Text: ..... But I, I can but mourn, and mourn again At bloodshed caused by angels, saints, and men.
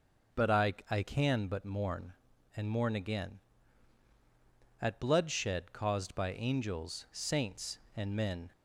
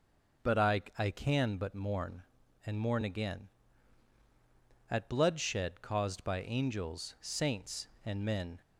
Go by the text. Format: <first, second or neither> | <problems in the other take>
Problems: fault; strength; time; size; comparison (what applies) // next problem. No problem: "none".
neither | starts louder than the rest; noticeable; the same in both